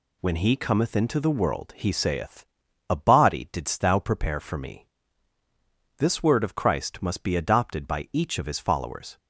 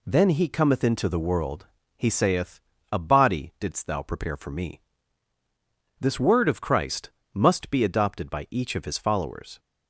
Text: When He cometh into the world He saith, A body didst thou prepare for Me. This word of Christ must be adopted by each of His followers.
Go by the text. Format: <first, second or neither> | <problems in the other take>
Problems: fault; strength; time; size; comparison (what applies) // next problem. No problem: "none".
first | says "Then" for "When"; at 0.0 s // pauses between "world" and "He"; slight; at 1.6 s; 0.30 s long // pauses between "Christ" and "must"; slight; at 7.0 s; 0.24 s long